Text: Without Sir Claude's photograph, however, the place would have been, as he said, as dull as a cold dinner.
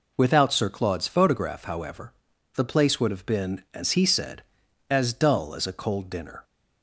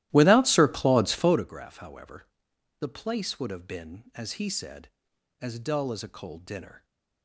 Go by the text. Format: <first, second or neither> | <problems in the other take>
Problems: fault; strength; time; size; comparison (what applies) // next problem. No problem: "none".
first | starts louder than the rest; strong; until 1.5 s; 15 dB